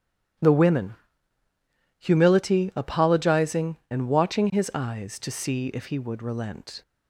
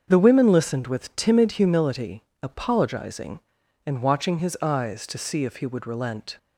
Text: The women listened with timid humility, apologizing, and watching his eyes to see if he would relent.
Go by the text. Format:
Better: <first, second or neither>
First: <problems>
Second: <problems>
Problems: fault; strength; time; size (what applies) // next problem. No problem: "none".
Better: second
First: starts louder than the rest; strong; until 2.4 s; 12 dB // skips "listened with timid"; at 1.4 s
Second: starts louder than the rest; until 1.0 s; 7 dB